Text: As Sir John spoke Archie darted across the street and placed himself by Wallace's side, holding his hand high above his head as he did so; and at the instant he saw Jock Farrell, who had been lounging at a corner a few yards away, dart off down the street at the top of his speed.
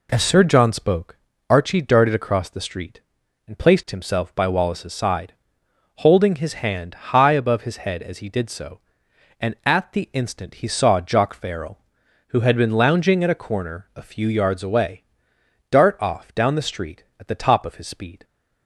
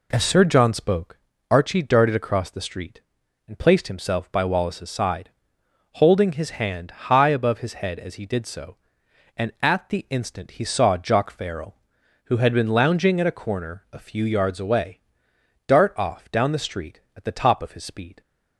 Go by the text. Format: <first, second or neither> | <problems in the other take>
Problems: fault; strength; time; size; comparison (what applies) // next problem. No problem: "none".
neither | pauses between "spoke" and "Archie"; slight; the same in both // pauses between "hand" and "high"; slight; the same in both